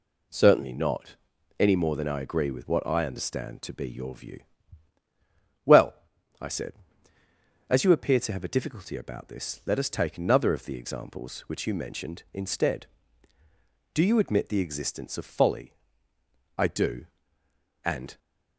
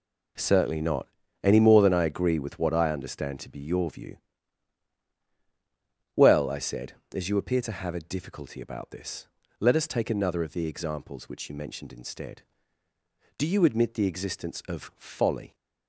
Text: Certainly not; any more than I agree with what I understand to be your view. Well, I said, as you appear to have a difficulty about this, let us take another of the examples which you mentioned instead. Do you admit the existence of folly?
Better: second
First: goes on to say "I do And"; from 16.5 s on; 1.6 s long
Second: none

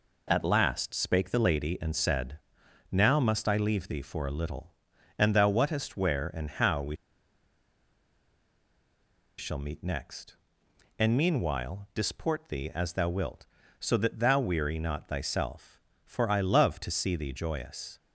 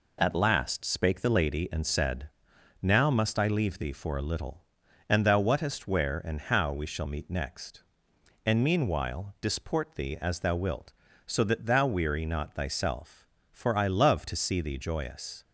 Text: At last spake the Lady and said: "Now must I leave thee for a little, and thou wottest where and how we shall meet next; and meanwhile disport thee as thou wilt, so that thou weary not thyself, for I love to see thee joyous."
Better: second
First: pauses between "we" and "shall"; strong; at 6.9 s; 2.4 s long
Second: none

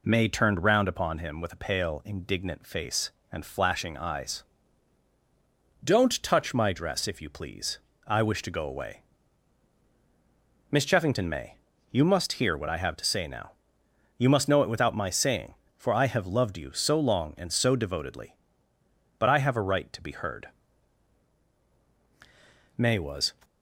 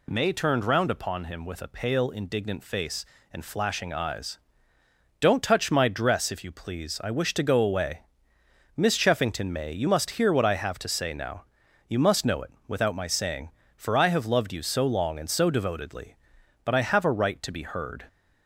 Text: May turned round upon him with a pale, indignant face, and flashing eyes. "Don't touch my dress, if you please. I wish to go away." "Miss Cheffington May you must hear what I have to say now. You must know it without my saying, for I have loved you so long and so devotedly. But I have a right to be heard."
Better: second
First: pauses between "May" and "you"; slight; at 11.5 s; 0.33 s long // goes on to say "May was"; from 22.7 s on; 0.56 s long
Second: none

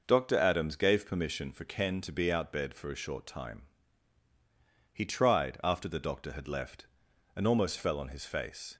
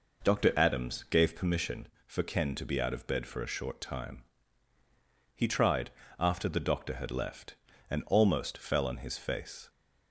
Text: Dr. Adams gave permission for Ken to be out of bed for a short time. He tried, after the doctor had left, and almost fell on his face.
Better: second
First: skips "of"; at 2.5 s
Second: none

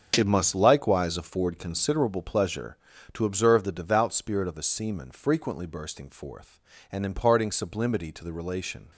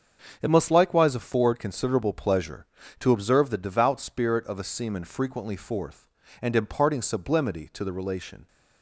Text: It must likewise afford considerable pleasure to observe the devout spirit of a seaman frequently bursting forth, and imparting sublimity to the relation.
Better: first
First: starts louder than the rest; strong; until 1.1 s; 7 dB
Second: starts louder than the rest; until 1.4 s; 7 dB // skips "bursting"; at 5.5 s

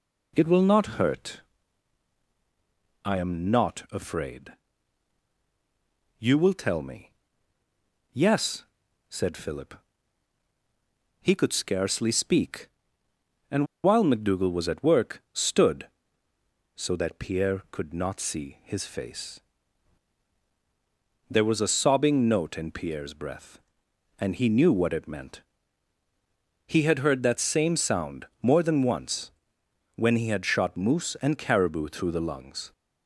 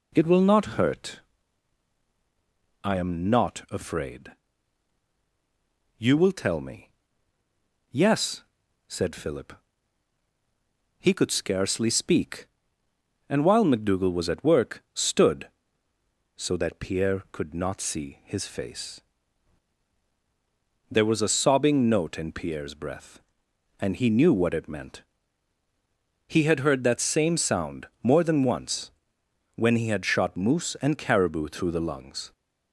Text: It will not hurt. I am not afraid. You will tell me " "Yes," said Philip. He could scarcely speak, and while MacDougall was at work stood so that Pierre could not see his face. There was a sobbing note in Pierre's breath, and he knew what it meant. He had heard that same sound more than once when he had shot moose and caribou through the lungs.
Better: second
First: pauses between "and" and "while"; slight; at 13.6 s; 0.19 s long // pauses between "sound" and "more"; slight; at 28.2 s; 0.16 s long // pauses between "once" and "when"; noticeable; at 29.3 s; 0.66 s long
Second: pauses between "sound" and "more"; slight; at 27.8 s; 0.16 s long // pauses between "once" and "when"; noticeable; at 28.8 s; 0.66 s long

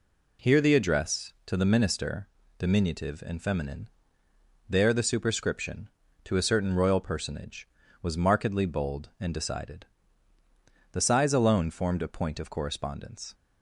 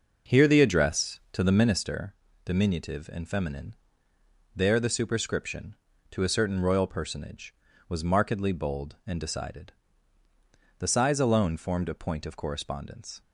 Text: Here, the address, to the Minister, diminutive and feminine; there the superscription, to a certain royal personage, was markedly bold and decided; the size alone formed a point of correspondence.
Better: first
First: none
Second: starts louder than the rest; noticeable; until 1.8 s; 5.5 dB

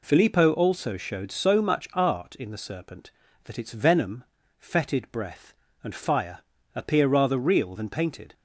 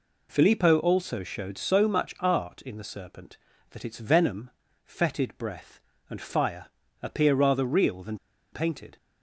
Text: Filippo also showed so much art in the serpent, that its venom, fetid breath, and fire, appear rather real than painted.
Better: first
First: none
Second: pauses between "than" and "painted"; at 8.1 s; 0.36 s long

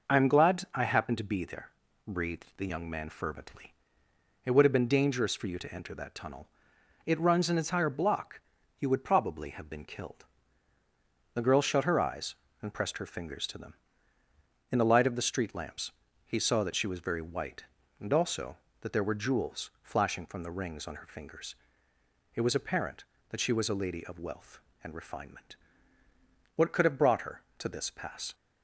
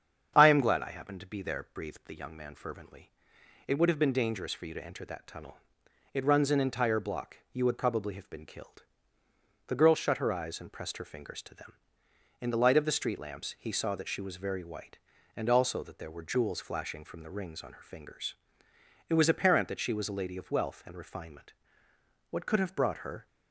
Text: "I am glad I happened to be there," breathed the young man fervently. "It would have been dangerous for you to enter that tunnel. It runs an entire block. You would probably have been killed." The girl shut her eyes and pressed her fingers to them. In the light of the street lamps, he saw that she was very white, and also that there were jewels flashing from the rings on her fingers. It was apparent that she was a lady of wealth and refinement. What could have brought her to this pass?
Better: first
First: none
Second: starts louder than the rest; strong; until 1.3 s; 7.5 dB // stops before "to this pass"; at 23.2 s

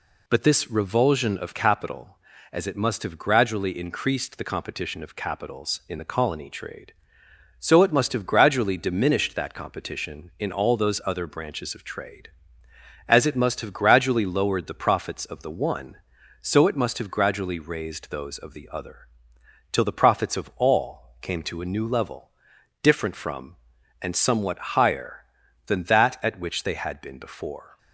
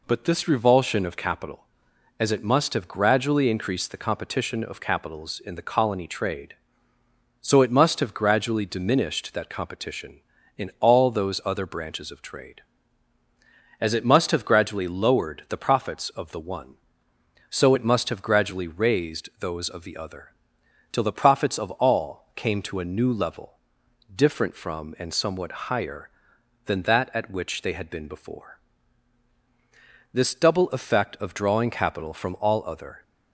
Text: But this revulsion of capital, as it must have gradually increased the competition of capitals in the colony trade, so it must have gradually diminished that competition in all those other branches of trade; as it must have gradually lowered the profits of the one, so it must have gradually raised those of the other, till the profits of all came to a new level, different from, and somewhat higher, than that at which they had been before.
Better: first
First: none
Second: goes on to say "This double effect of drawing capital from all other"; strong; from 30.1 s on; 2.8 s long

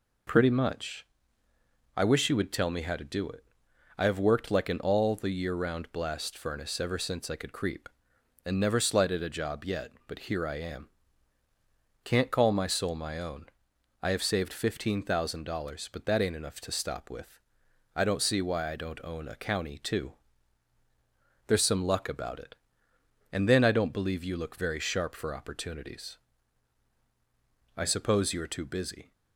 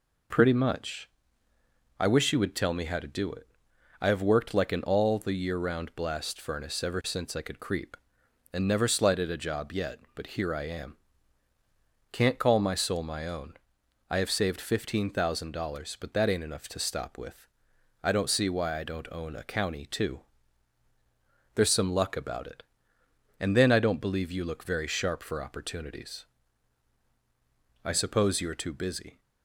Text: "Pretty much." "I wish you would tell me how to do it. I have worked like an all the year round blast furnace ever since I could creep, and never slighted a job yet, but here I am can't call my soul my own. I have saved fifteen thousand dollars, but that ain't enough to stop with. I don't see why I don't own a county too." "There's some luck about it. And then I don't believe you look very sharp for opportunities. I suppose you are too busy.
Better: neither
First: pauses between "am" and "can't"; at 10.9 s; 1.1 s long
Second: pauses between "am" and "can't"; at 10.9 s; 1.1 s long

